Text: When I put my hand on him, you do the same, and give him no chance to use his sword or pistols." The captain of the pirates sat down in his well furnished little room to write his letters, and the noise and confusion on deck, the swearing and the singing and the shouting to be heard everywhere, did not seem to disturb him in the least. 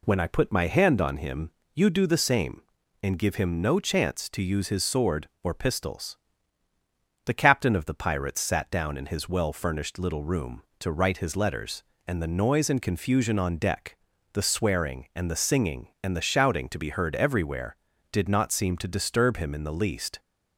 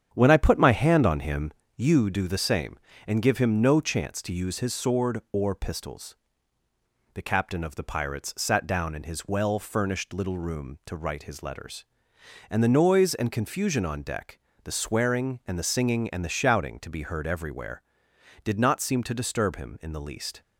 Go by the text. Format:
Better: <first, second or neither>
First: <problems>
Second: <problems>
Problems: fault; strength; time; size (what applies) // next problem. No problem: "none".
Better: first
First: none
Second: starts louder than the rest; strong; until 1.5 s; 8.5 dB